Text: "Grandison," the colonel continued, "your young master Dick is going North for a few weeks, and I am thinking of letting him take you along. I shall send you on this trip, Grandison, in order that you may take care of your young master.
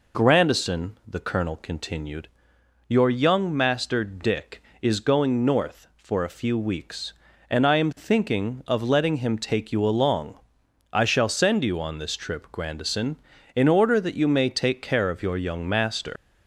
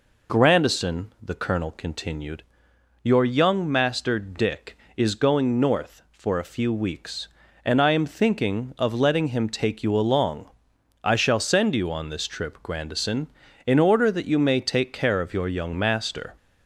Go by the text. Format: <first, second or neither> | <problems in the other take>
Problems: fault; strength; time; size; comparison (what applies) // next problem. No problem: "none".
second | leaves "master" unfinished; at 16.1 s; 100 ms